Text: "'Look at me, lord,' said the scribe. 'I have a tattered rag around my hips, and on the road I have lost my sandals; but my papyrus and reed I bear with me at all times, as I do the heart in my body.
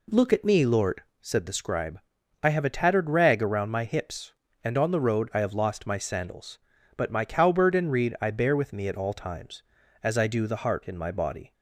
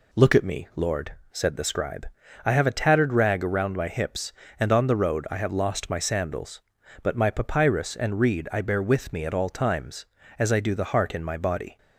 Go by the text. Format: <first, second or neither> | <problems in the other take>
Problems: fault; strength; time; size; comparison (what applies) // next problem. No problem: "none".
second | says "cowbird" for "papyrus"; at 7.2 s